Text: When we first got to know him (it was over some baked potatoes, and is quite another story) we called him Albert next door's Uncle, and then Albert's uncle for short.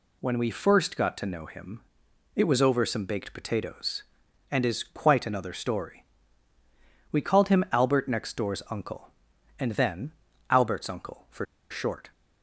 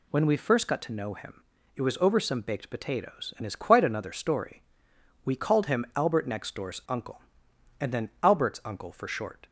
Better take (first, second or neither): second